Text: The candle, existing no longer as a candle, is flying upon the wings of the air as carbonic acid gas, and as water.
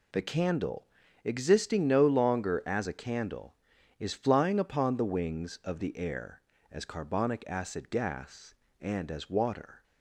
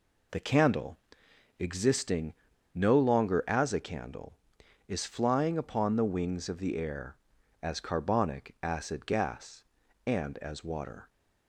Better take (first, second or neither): first